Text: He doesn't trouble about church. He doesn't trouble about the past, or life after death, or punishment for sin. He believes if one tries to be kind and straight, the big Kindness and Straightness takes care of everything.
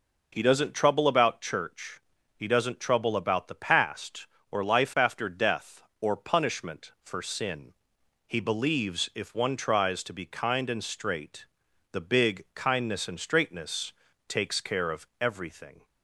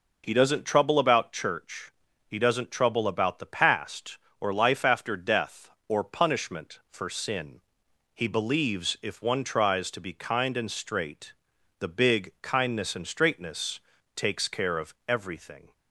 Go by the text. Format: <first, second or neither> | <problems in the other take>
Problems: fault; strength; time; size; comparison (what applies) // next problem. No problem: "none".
neither | pauses between "Straightness" and "takes"; slight; the same in both